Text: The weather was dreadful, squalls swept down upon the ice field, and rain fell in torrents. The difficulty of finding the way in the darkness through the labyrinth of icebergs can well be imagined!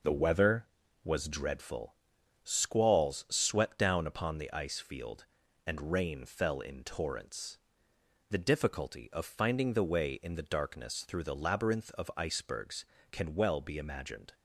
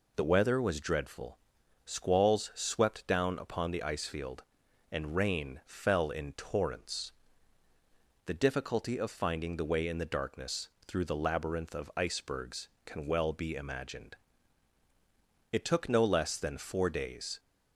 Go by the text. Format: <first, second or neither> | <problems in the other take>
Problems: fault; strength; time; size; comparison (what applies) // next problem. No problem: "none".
first | pauses between "darkness" and "through"; slight; at 10.6 s; 0.18 s long // goes on to say "It took no less than four days"; strong; from 15.5 s on; 1.8 s long